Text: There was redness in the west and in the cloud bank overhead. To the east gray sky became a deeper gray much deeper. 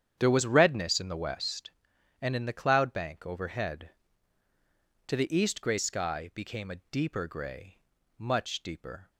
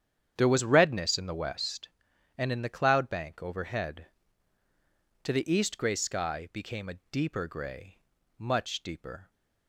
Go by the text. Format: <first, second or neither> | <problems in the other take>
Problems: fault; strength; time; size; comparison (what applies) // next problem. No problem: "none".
neither | starts louder than the rest; strong; the same in both // pauses between "gray" and "much"; the same in both